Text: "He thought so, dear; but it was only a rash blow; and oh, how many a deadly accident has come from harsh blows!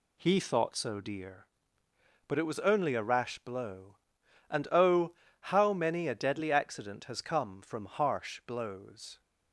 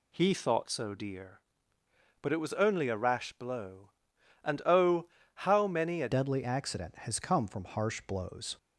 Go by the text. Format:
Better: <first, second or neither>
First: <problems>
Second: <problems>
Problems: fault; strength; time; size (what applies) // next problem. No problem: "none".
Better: first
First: none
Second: changes voice at "deadly"; from 6.1 s on; 2.4 s long